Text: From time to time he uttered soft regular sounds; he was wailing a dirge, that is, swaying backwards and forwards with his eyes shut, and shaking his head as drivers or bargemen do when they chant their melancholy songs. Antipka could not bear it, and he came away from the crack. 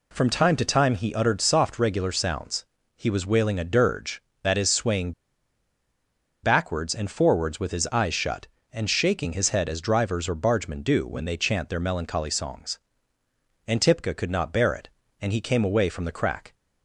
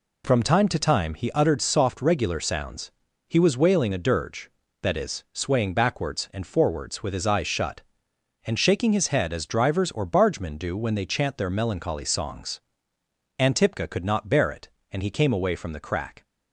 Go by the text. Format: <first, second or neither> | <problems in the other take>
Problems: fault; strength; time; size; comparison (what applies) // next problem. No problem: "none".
second | pauses between "swaying" and "backwards"; strong; at 5.1 s; 1.3 s long